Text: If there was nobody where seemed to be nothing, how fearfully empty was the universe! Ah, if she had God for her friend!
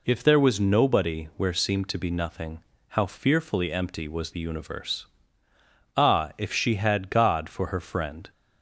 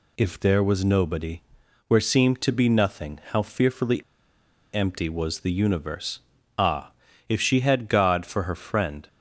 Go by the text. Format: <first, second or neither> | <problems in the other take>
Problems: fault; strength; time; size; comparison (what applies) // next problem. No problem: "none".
first | pauses between "nobody" and "where"; noticeable; at 1.4 s; 0.46 s long // pauses between "fearfully" and "empty"; noticeable; at 4.0 s; 0.71 s long